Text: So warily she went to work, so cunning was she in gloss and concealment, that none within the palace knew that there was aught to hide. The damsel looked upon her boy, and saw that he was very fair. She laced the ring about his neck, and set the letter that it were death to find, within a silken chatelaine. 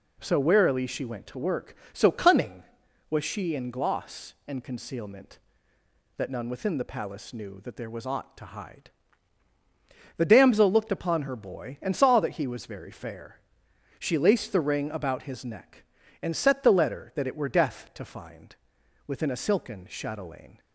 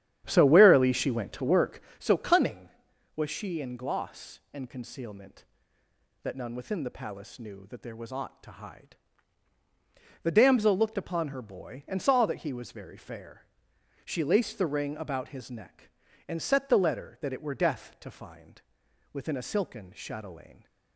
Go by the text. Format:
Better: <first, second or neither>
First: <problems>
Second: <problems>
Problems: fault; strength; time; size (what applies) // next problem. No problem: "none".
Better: first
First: none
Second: starts louder than the rest; strong; until 2.0 s; 10.5 dB